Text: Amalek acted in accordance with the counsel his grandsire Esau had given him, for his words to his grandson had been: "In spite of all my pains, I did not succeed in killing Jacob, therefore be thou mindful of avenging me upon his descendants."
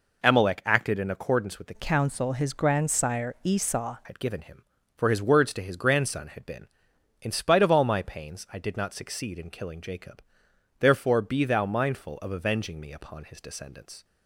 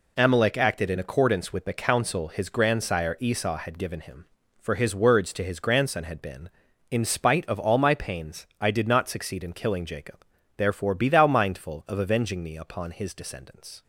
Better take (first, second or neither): second